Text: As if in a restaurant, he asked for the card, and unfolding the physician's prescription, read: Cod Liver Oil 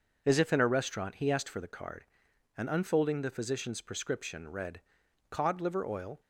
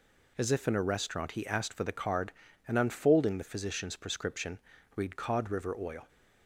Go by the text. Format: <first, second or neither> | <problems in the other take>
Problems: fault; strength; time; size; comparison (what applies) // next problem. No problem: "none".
first | says "River" for "Liver"; at 5.5 s